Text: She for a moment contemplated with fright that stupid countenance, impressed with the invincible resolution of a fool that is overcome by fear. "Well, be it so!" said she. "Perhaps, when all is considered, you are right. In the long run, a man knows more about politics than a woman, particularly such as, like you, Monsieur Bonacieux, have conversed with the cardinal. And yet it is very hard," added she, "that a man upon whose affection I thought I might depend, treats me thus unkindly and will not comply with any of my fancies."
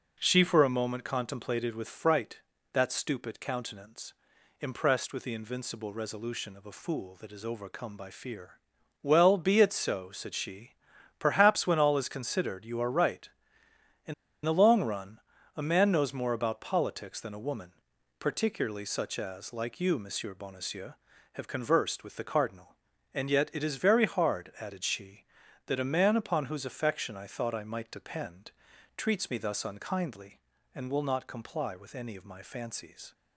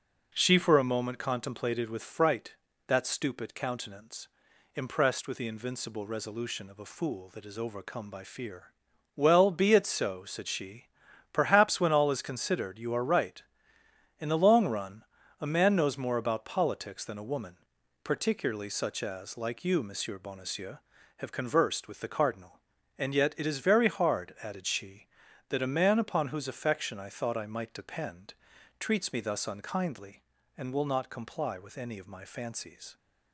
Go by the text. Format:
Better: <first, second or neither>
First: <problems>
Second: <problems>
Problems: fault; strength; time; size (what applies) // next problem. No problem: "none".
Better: second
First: pauses between "In" and "the"; slight; at 14.1 s; 0.31 s long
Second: none